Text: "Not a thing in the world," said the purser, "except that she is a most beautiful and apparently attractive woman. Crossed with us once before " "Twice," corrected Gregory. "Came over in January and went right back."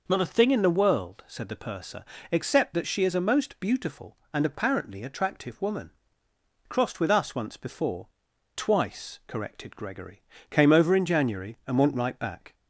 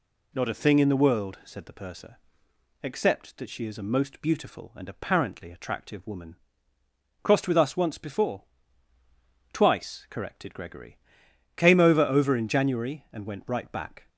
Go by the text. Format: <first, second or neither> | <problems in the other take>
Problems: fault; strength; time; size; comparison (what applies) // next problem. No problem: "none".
first | says "over" twice; at 12.0 s